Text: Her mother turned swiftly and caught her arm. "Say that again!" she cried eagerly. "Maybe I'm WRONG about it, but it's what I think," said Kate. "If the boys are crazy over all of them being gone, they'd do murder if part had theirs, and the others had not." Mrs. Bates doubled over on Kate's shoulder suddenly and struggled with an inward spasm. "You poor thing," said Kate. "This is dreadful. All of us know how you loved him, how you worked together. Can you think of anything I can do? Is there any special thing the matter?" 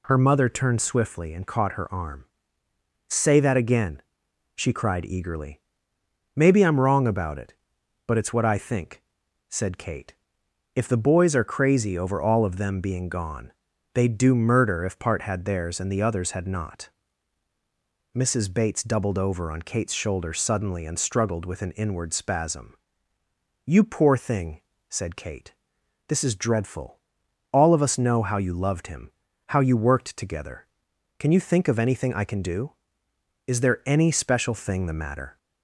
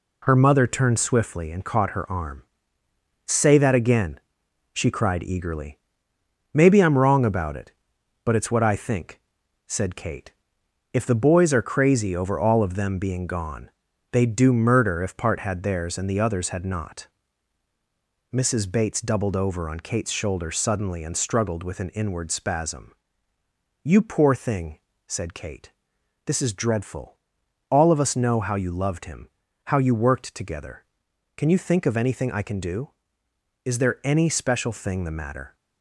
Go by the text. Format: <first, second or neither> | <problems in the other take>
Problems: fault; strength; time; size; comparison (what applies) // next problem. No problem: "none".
first | gets quieter; noticeable; throughout; 5 dB